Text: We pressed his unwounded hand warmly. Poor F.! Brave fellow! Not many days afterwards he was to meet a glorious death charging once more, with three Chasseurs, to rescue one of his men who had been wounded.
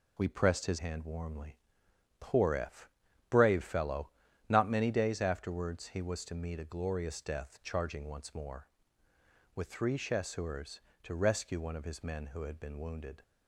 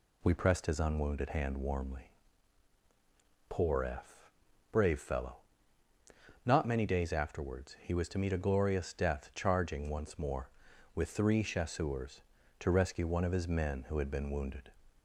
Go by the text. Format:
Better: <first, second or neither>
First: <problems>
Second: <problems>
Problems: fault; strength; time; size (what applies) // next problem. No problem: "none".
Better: second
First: skips "unwounded"; at 0.7 s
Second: none